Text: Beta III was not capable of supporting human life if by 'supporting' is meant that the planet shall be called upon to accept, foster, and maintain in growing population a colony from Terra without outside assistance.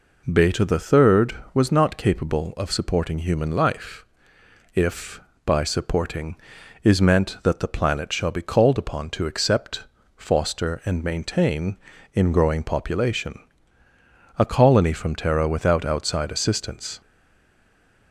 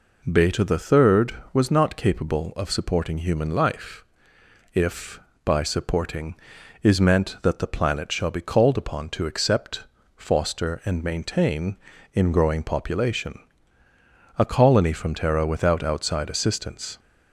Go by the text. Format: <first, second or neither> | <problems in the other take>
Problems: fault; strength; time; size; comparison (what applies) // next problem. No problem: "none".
second | pauses between "life" and "if"; noticeable; at 4.0 s; 0.68 s long; noticeable in the second // pauses between "population" and "a"; at 13.3 s; 1.0 s long; also in the second // stays silent after the last word; from 17.0 s on; 1.1 s long